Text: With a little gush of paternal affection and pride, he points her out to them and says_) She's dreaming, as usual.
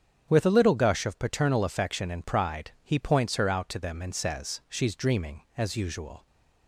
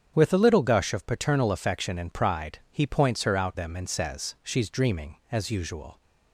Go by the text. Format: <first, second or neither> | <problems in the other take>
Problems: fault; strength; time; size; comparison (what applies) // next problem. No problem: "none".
first | starts louder than the rest; strong; until 1.1 s; 8 dB; strong in the first // skips "to"; at 3.5 s